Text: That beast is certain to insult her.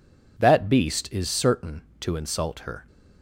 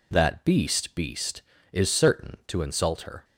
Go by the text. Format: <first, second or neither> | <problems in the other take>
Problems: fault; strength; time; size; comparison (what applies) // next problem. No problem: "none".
first | says "beast" twice; at 0.9 s